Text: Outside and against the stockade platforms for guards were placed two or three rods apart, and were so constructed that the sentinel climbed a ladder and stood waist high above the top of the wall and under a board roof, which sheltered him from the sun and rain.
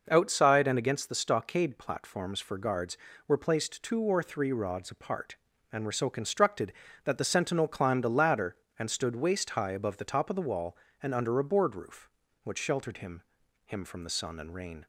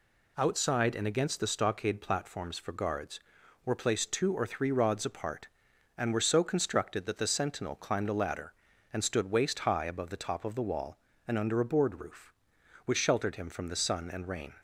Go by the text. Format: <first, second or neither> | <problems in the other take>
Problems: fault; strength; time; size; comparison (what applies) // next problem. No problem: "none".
second | says "him" twice; at 13.6 s